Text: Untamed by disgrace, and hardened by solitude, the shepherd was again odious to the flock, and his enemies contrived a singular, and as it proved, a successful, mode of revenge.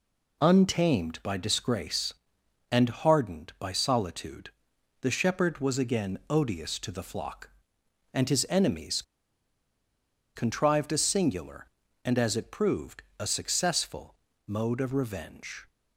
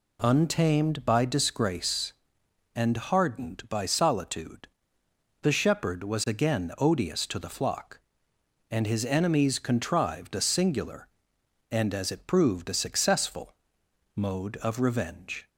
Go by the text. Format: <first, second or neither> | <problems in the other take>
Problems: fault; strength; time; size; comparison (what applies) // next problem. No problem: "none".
second | pauses between "enemies" and "contrived"; strong; at 9.0 s; 1.3 s long